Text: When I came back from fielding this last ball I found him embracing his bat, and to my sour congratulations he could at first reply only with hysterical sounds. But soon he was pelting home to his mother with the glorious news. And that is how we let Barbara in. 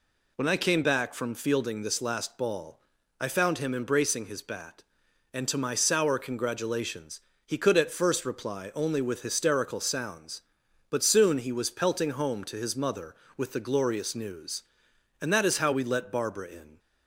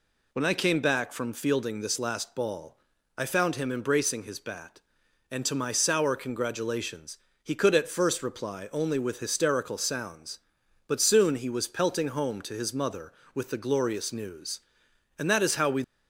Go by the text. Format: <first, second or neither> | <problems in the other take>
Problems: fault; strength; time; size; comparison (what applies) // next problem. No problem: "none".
first | pauses between "ball" and "I"; at 2.7 s; 0.42 s long; also in the first // pauses between "congratulations" and "he"; slight; at 7.1 s; 0.24 s long; slight in the first // stops before "let Barbara in"; at 15.8 s